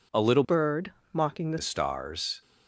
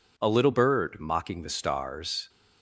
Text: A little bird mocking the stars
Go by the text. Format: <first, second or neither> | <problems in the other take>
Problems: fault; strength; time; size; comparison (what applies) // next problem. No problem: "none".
second | changes voice from "bird" to "the"; from 0.4 to 1.5 s; 1.1 s long // pauses between "bird" and "mocking"; slight; at 0.9 s; 0.20 s long